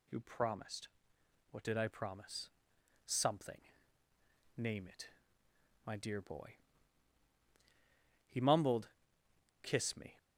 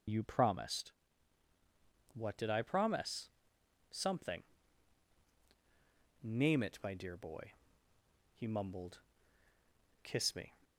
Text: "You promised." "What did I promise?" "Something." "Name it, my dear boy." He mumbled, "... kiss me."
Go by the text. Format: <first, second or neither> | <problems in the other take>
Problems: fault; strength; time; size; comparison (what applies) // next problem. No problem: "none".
first | loses the start of "You"; at 0.0 s; 45 ms // starts louder than the rest; strong; until 2.3 s; 7 dB